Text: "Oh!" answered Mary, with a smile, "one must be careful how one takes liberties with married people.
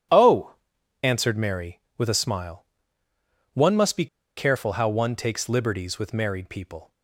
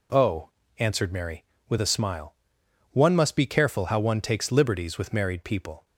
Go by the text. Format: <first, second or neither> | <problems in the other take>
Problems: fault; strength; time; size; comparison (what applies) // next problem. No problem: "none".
second | pauses between "be" and "careful"; slight; at 4.0 s; 0.30 s long